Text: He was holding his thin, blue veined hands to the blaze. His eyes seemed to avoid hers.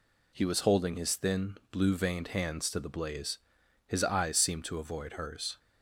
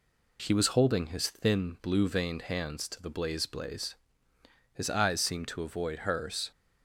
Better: first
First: none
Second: says "blaze" twice; at 3.4 s

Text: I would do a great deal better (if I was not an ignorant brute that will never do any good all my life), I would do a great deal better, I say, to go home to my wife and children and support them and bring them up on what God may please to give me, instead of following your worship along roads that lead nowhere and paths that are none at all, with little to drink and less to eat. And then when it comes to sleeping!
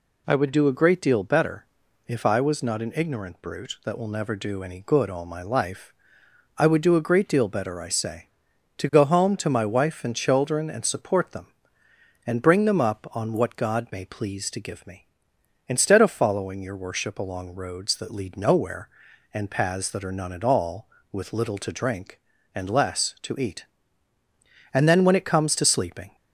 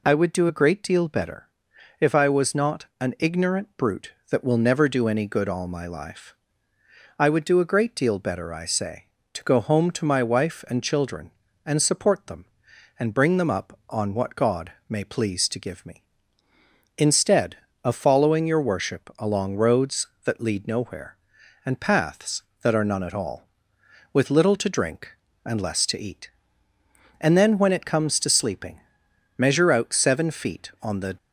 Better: first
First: none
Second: pauses between "God" and "may"; slight; at 14.7 s; 0.18 s long // goes on to say "Measure out seven feet on the"; strong; from 29.3 s on; 1.8 s long

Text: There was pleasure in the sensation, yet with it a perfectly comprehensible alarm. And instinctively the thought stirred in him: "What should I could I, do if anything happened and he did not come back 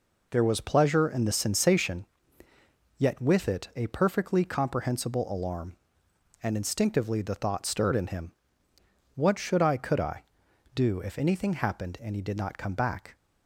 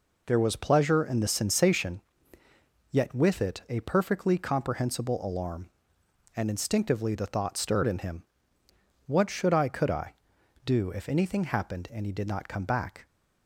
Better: neither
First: none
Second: none

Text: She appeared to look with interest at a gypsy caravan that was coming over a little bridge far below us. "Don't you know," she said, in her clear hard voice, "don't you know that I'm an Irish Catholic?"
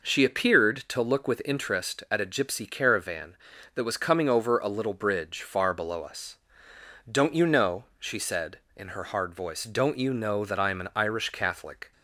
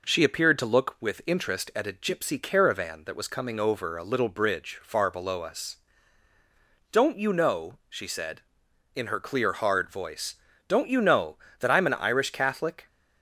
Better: second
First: skips "clear"; at 9.0 s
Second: none

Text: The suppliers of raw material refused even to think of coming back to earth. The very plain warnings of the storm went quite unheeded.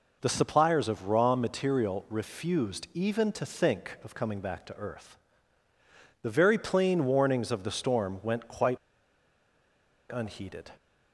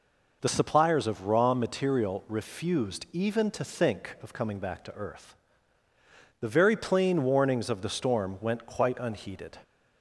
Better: second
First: pauses between "quite" and "unheeded"; strong; at 8.7 s; 1.3 s long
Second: none

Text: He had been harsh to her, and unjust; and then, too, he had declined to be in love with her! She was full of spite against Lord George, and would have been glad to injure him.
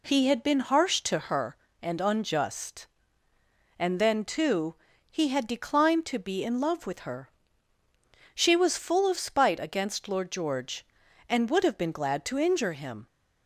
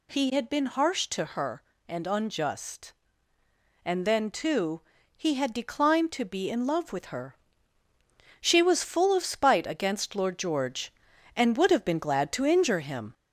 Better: first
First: none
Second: gets louder; slight; throughout; 2.5 dB

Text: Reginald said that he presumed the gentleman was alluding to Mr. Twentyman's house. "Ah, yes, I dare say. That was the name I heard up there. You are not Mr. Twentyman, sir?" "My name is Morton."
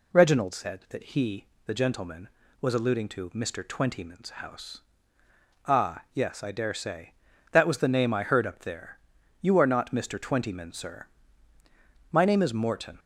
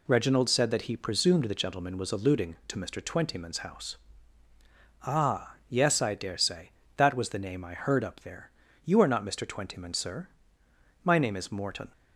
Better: second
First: skips "presumed"; at 1.5 s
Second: none

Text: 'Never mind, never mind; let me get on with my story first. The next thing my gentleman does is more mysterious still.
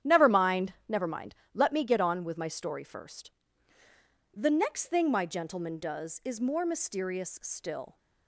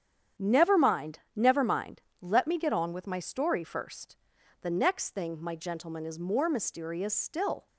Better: first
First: starts louder than the rest; strong; until 1.1 s; 9.5 dB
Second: starts louder than the rest; strong; until 1.5 s; 8.5 dB // skips "does"; at 6.0 s

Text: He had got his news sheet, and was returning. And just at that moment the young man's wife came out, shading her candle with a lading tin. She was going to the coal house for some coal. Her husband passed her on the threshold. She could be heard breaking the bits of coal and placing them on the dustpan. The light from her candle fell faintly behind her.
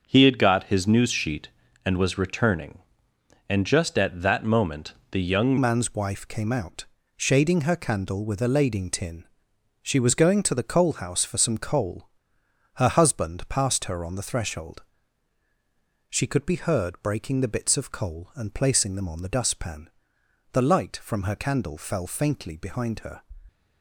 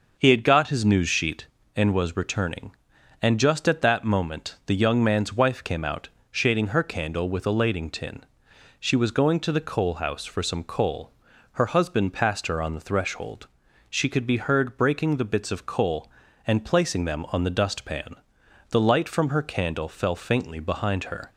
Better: second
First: starts louder than the rest; until 1.0 s; 6 dB // pauses between "moment" and "the"; slight; at 4.9 s; 0.18 s long // changes voice at "man's"; from 5.5 s on; 17.7 s long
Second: starts louder than the rest; noticeable; until 1.1 s; 6 dB

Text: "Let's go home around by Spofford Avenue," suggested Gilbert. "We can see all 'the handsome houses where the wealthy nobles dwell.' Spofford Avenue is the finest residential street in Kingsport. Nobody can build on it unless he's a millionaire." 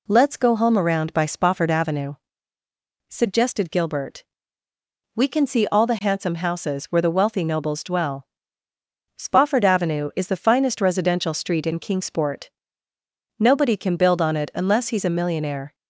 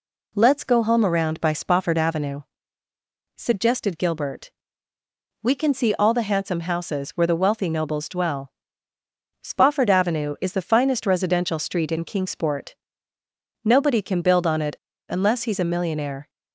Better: first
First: none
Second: pauses between "it" and "unless"; slight; at 14.7 s; 0.33 s long

